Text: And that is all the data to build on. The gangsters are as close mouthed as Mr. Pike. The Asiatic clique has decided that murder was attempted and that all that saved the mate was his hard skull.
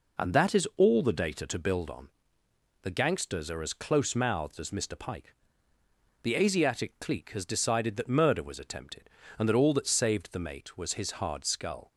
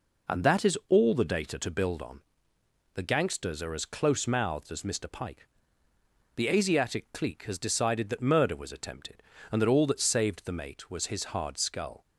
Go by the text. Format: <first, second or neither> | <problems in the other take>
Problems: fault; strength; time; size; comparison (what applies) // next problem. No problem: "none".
neither | none